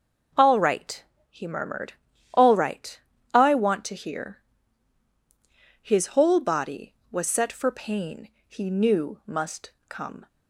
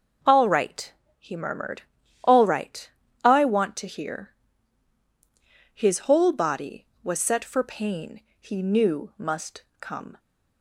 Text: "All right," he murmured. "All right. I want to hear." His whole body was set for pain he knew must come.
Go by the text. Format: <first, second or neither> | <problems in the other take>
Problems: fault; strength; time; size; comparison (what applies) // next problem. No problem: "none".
neither | pauses between "pain" and "he"; slight; the same in both // pauses between "must" and "come"; slight; the same in both